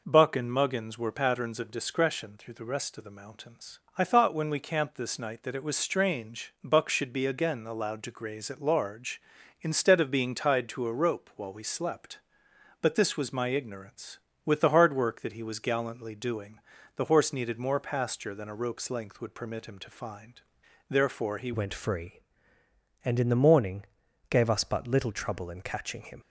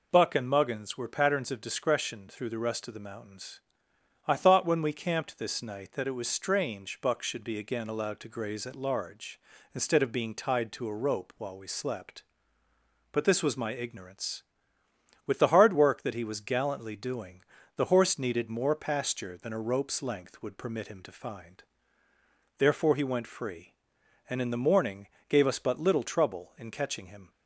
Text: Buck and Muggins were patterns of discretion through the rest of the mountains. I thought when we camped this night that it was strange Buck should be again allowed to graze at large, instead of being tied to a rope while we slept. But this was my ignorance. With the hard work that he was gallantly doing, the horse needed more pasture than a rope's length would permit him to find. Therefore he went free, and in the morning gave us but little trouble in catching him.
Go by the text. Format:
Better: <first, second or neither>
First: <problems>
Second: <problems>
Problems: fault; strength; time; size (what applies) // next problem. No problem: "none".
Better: second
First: changes voice at "went"; from 21.5 s on; 4.7 s long // pauses between "morning" and "gave"; at 23.8 s; 0.44 s long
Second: pauses between "morning" and "gave"; slight; at 25.0 s; 0.22 s long